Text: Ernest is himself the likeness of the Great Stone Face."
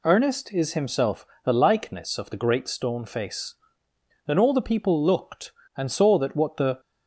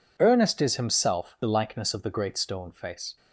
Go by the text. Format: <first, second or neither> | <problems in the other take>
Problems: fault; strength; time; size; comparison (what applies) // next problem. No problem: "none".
second | pauses between "himself" and "the"; slight; at 1.2 s; 0.18 s long // goes on to say "Then all the people looked and saw that what the"; strong; from 4.2 s on; 2.5 s long